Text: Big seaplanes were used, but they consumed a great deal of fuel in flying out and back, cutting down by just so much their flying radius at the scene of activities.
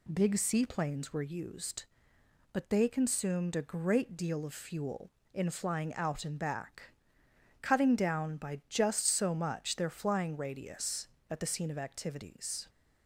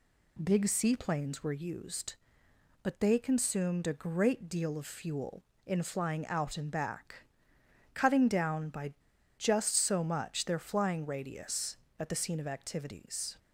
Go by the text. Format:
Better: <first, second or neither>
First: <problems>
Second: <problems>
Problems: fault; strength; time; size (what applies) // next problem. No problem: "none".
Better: first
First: none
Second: pauses between "by" and "just"; at 8.9 s; 0.44 s long